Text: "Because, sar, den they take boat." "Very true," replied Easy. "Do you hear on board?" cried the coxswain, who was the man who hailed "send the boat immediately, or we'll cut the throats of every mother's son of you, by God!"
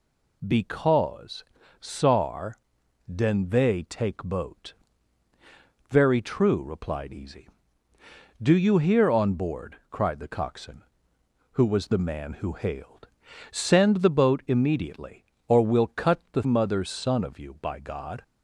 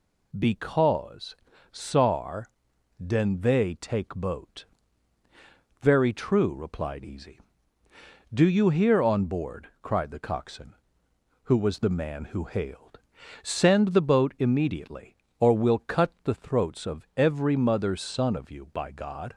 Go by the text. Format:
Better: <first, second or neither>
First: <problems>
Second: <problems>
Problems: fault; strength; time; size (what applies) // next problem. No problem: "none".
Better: second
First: pauses between "hailed" and "send"; at 13.0 s; 0.42 s long // skips "throats of every"; at 16.4 s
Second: pauses between "hailed" and "send"; at 13.0 s; 0.42 s long